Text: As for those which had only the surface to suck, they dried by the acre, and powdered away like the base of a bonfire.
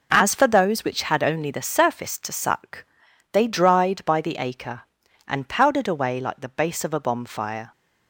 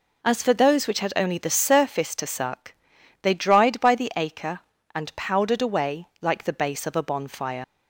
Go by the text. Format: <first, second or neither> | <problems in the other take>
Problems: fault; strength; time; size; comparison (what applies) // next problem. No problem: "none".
first | leaves "bonfire" unfinished; at 7.6 s; 65 ms